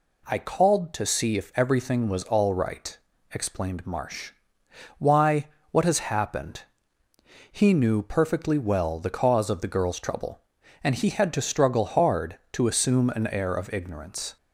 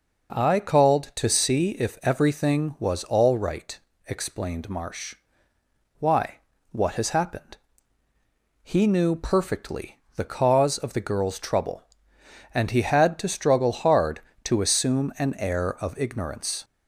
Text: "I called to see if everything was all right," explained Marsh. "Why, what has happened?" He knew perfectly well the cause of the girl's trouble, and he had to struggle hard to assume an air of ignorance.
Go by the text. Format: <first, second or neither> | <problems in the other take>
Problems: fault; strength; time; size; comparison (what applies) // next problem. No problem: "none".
first | skips "well"; at 10.0 s